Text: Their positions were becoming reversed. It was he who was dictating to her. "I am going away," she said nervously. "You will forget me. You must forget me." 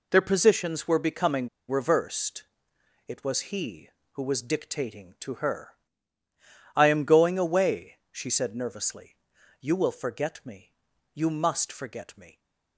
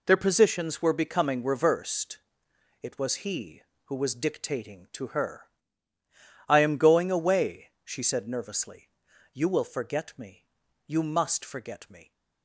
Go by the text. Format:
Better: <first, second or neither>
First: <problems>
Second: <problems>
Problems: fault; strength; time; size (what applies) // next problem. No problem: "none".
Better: second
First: pauses between "becoming" and "reversed"; slight; at 1.4 s; 0.20 s long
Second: none